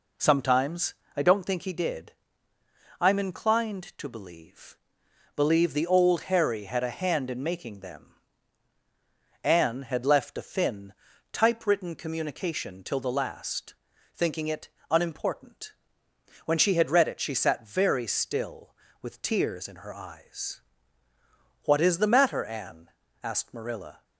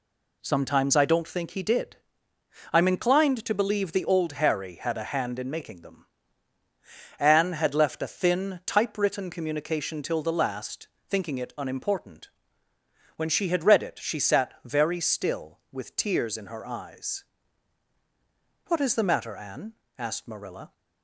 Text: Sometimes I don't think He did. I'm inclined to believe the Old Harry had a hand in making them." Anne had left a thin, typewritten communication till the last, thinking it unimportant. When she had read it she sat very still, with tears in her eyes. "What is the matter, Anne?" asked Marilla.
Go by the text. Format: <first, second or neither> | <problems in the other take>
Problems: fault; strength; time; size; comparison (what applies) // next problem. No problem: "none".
second | pauses between "Sometimes" and "I"; slight; at 0.9 s; 0.22 s long // says "believe" twice; at 5.3 s // pauses between "it" and "unimportant"; slight; at 14.6 s; 0.24 s long